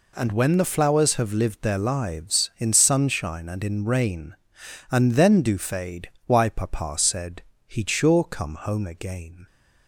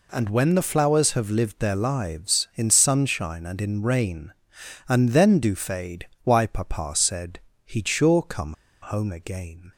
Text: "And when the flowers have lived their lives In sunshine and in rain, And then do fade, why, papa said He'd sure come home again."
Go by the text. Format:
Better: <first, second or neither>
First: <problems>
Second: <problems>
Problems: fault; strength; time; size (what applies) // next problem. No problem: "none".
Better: first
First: pauses between "said" and "He'd"; slight; at 7.4 s; 0.25 s long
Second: pauses between "said" and "He'd"; slight; at 7.3 s; 0.26 s long // pauses between "come" and "home"; slight; at 8.5 s; 0.27 s long